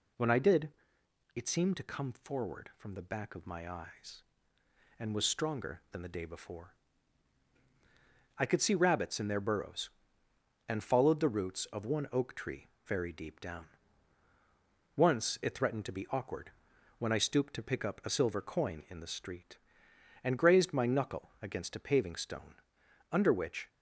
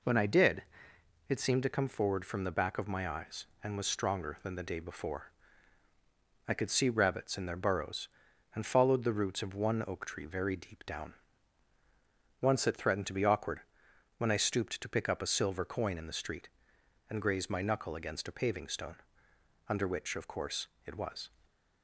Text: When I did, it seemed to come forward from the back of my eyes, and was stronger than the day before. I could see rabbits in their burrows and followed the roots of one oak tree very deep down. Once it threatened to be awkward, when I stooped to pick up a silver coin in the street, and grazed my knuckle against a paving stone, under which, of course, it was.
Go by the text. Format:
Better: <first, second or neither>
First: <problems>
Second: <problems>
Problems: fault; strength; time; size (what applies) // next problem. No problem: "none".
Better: second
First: pauses between "tree" and "very"; slight; at 12.6 s; 0.20 s long // stops before "of course it was"; at 23.6 s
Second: none